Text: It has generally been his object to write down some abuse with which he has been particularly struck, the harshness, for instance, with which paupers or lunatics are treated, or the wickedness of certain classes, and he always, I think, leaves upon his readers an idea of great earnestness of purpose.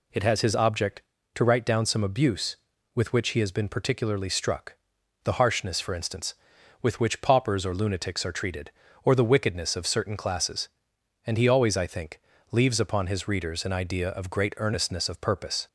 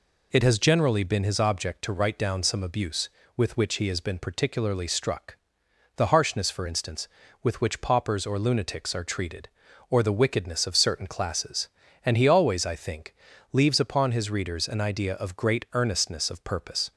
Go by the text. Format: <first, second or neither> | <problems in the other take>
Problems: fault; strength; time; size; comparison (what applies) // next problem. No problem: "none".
second | skips "generally been"; at 0.4 s